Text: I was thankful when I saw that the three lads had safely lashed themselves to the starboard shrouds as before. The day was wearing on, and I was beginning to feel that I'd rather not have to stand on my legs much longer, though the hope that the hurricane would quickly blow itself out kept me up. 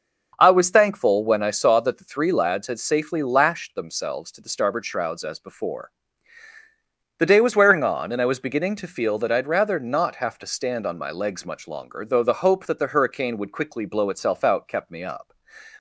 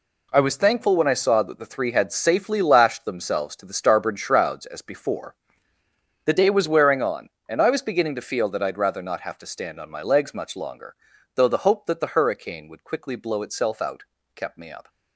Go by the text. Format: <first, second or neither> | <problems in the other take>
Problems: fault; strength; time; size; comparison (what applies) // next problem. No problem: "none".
first | skips "lads"; at 1.9 s // pauses between "out" and "kept"; slight; at 14.0 s; 0.32 s long